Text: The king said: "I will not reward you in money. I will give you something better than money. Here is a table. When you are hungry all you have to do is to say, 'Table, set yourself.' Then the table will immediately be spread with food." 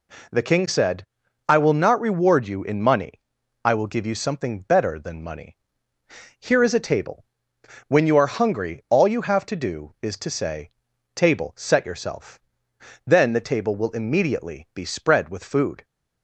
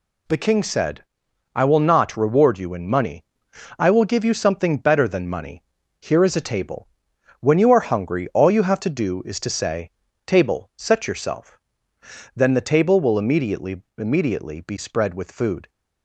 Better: first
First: none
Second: says "immediately" twice; at 13.9 s

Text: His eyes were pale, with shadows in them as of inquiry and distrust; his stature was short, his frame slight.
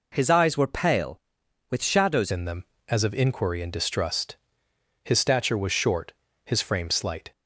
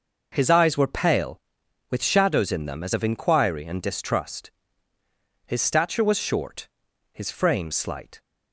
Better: second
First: changes voice at "in"; from 2.2 s on; 5.1 s long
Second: none

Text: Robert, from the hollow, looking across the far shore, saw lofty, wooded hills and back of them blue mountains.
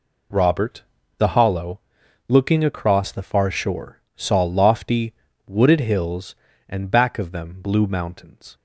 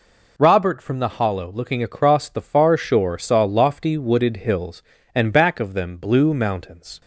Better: second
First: skips "from"; at 1.0 s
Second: none

